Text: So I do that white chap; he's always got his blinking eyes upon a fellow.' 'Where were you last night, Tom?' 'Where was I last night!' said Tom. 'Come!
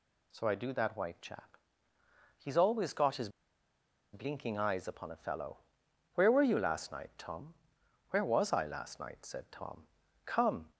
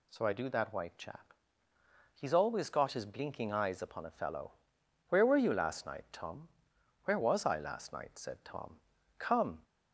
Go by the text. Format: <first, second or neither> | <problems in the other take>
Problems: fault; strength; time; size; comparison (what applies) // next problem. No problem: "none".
second | pauses between "his" and "blinking"; noticeable; at 3.2 s; 0.84 s long